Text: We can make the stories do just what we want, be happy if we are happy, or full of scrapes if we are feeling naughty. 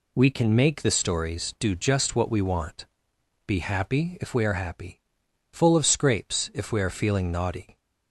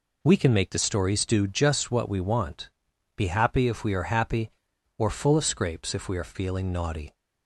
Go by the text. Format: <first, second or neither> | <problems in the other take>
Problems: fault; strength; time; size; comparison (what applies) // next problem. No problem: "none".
second | skips "or"; at 5.2 s